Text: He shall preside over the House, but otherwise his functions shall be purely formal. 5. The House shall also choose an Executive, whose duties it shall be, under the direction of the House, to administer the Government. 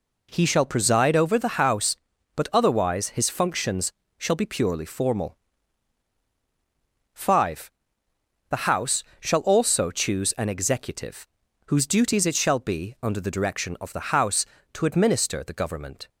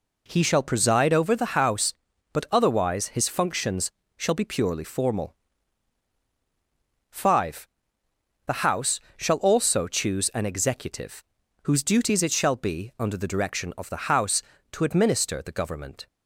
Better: neither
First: pauses between "functions" and "shall"; slight; at 3.9 s; 0.26 s long // pauses between "House" and "shall"; slight; at 9.0 s; 0.16 s long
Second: pauses between "functions" and "shall"; slight; at 3.9 s; 0.26 s long // pauses between "House" and "shall"; slight; at 9.0 s; 0.16 s long

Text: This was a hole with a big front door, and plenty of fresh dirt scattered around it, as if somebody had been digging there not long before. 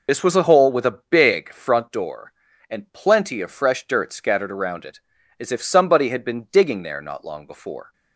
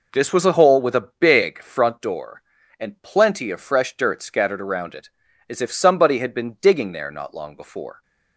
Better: second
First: loses the start of "This"; at 0.0 s; 65 ms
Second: none

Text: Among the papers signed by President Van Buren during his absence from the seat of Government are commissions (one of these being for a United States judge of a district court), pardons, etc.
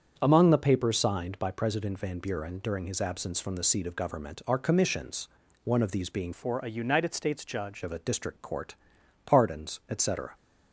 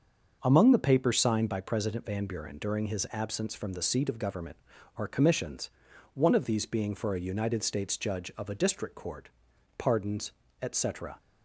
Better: second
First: starts louder than the rest; strong; until 1.1 s; 7.5 dB // changes voice from "for" to "judge"; from 6.3 to 7.8 s; 1.5 s long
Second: starts louder than the rest; until 1.4 s; 6.5 dB

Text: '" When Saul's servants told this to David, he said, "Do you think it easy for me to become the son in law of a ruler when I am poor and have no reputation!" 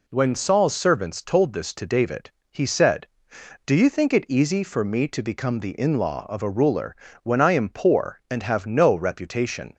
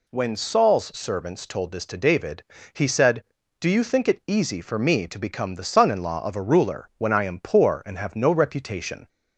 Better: second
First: skips "son"; at 5.7 s // pauses between "ruler" and "when"; slight; at 6.9 s; 0.28 s long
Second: none

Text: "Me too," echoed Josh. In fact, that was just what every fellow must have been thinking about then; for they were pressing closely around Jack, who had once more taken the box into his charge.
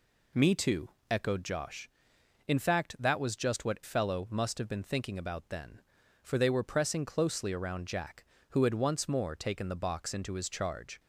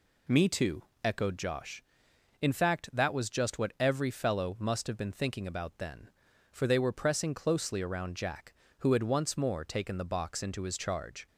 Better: second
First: skips "every"; at 3.8 s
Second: none

